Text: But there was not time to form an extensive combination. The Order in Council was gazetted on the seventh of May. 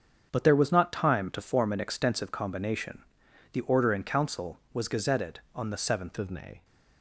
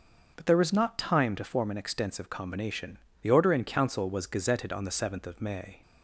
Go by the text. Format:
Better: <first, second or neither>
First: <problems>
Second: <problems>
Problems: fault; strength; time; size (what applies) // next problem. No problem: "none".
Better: second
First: starts louder than the rest; until 1.3 s; 7 dB // changes voice at "of"; from 6.1 s on; 0.5 s long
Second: starts louder than the rest; until 1.3 s; 6 dB